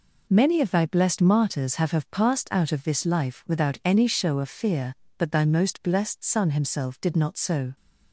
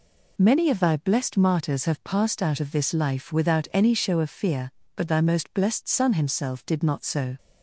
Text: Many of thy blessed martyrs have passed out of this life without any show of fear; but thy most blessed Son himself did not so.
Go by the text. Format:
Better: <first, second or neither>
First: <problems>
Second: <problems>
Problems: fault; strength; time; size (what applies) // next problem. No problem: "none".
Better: second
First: says "have" twice; at 1.9 s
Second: none